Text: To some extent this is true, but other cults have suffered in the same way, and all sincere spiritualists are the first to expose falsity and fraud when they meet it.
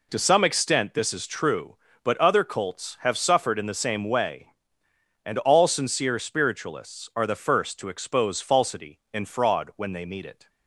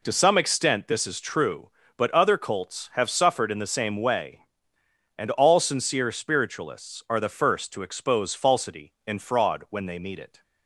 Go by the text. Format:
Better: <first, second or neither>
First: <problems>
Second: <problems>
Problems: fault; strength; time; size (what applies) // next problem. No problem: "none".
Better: neither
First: none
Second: none